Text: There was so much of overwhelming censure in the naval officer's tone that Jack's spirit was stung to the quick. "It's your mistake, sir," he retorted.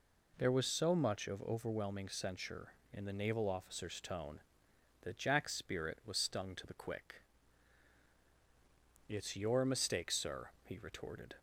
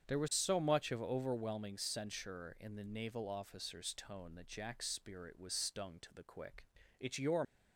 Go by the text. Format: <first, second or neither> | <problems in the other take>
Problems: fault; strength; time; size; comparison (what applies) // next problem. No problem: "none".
first | starts louder than the rest; strong; until 1.1 s; 7.5 dB // stops before "mistake sir he retorted"; at 7.4 s